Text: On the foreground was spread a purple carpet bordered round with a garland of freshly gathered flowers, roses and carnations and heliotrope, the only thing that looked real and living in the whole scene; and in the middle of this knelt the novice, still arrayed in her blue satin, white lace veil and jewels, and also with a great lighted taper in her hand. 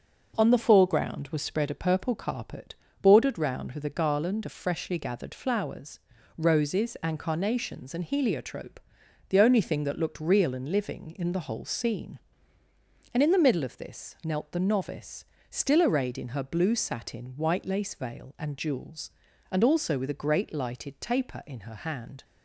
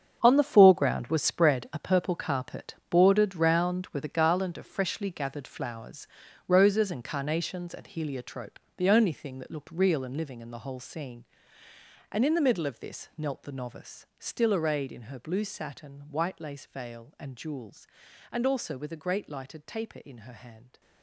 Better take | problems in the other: first | gets quieter; strong; throughout; 13 dB // pauses between "carpet" and "bordered"; slight; at 2.7 s; 0.16 s long; slight in the first

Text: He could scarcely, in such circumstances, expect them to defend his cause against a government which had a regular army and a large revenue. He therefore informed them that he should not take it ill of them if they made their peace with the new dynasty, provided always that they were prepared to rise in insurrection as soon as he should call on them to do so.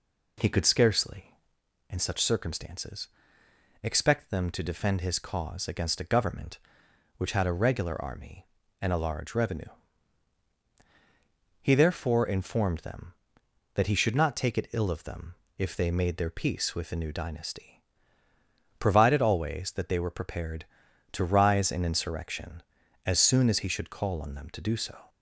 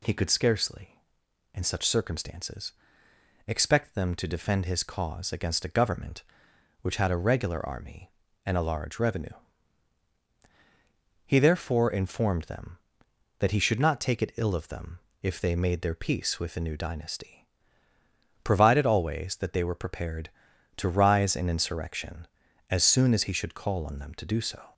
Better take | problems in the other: second | starts louder than the rest; slight; until 1.6 s; 3 dB // pauses between "them" and "if"; slight; at 15.3 s; 0.22 s long; slight in the second

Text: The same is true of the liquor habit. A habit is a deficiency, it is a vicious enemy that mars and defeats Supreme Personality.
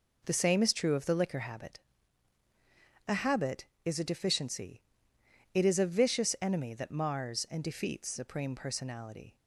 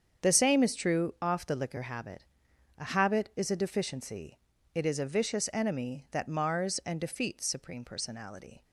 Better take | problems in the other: first | starts louder than the rest; strong; until 1.3 s; 7.5 dB // says "off" for "of"; at 1.2 s

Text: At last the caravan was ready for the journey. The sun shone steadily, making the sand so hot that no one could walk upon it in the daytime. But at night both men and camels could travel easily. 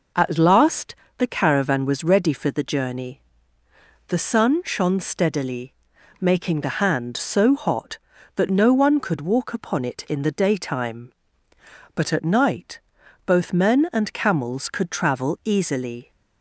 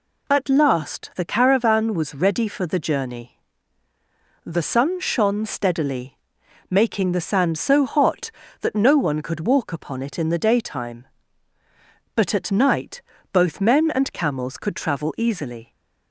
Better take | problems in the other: second | pauses between "last" and "the"; slight; at 0.9 s; 0.24 s long // says "hand" for "sand"; at 6.8 s // pauses between "night" and "both"; at 12.8 s; 0.44 s long; slight in the second

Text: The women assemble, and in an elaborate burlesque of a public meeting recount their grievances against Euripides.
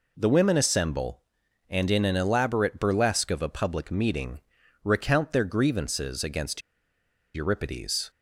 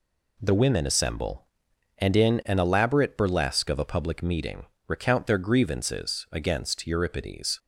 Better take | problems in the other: second | pauses between "meeting" and "recount"; at 4.4 s; 0.42 s long; slight in the second // pauses between "against" and "Euripides"; noticeable; at 6.6 s; 0.74 s long

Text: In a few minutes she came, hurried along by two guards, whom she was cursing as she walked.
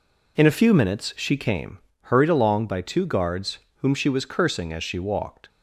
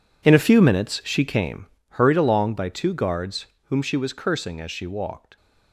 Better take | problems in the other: first | gets quieter; strong; throughout; 15 dB

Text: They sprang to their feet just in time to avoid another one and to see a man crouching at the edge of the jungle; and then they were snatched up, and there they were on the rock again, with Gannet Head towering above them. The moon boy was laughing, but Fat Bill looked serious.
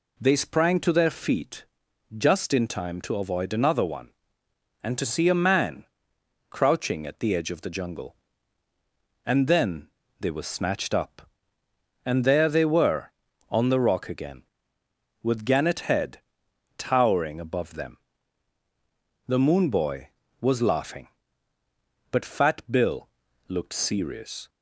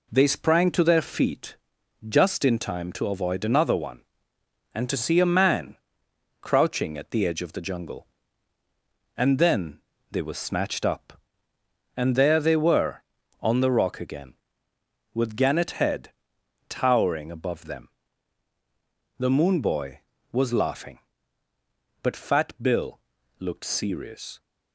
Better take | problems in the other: first | gets quieter; throughout; 4 dB // pauses between "feet" and "just"; noticeable; at 1.5 s; 0.52 s long; noticeable in the first // pauses between "man" and "crouching"; noticeable; at 5.7 s; 0.64 s long; noticeable in the first // pauses between "then" and "they"; slight; at 9.7 s; 0.30 s long; slight in the first // pauses between "Head" and "towering"; noticeable; at 16.0 s; 0.68 s long; noticeable in the first // pauses between "Fat" and "Bill"; slight; at 22.4 s; 0.16 s long; slight in the first // pauses between "Bill" and "looked"; at 22.9 s; 0.42 s long; also in the first

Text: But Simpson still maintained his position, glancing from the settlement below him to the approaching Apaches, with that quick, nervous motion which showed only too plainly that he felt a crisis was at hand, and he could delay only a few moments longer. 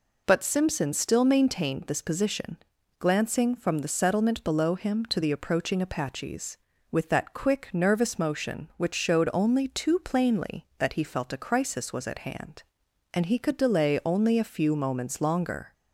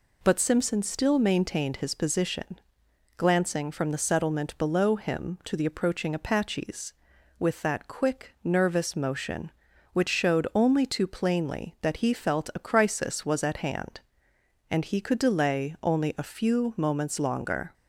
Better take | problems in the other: second | says "this" for "his"; at 1.8 s

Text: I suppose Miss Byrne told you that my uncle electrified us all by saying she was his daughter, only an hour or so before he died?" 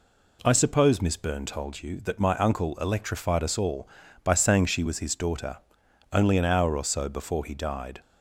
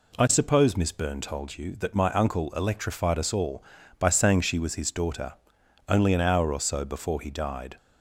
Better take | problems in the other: neither | none

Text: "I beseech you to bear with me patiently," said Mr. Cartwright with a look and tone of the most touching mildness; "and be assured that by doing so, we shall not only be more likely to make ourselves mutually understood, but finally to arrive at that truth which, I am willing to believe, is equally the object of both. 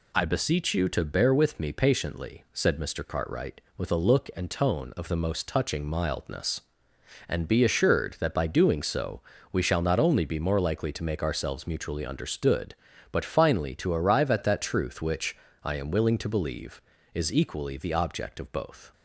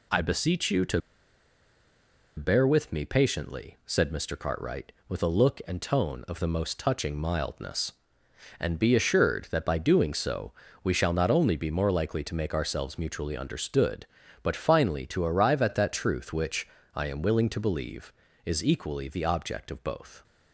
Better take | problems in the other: first | pauses between "to" and "bear"; strong; at 1.0 s; 1.3 s long

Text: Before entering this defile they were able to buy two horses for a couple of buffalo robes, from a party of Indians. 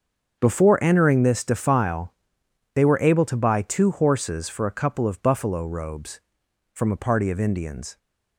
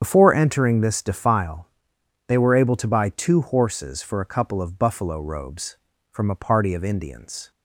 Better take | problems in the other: first | loses the start of "Before"; at 0.0 s; 55 ms // starts louder than the rest; strong; until 1.0 s; 8 dB; also in the first // pauses between "defile" and "they"; noticeable; at 1.6 s; 0.58 s long; noticeable in the first

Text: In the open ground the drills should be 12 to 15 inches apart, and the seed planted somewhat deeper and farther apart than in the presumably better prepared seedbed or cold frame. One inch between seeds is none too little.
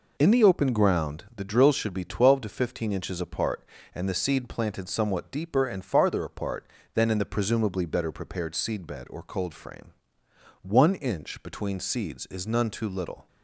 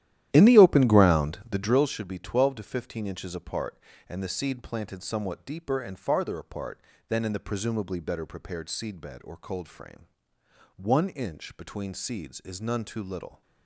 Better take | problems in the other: first | starts louder than the rest; strong; until 1.8 s; 12.5 dB

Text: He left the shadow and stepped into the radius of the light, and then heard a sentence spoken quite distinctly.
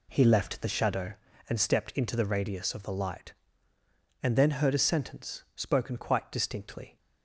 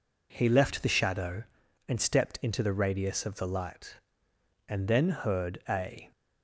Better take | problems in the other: first | stops before "sentence spoken quite distinctly"; at 6.1 s

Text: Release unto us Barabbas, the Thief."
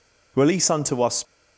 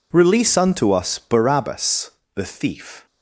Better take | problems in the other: second | stops before "Barabbas the Thief"; at 1.2 s

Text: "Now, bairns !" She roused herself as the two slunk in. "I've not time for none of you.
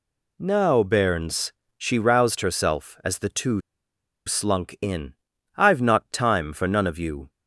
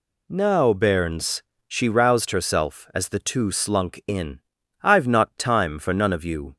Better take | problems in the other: second | pauses between "two" and "slunk"; noticeable; at 3.6 s; 0.66 s long

